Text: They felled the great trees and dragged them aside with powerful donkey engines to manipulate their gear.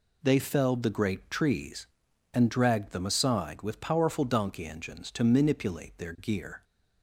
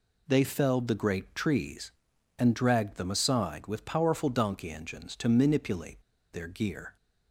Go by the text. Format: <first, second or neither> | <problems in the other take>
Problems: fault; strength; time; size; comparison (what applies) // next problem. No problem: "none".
first | pauses between "manipulate" and "their"; slight; at 6.0 s; 0.30 s long